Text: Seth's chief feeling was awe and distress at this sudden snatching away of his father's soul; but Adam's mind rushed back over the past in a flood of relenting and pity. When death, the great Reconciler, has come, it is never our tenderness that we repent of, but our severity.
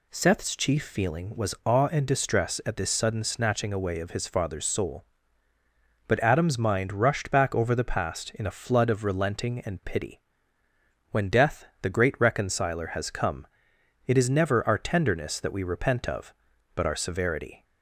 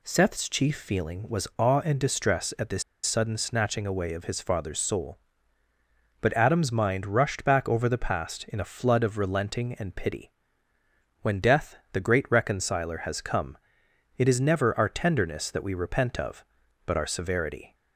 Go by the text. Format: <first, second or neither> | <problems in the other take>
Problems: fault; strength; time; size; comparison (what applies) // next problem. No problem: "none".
first | pauses between "this" and "sudden"; slight; at 2.8 s; 0.21 s long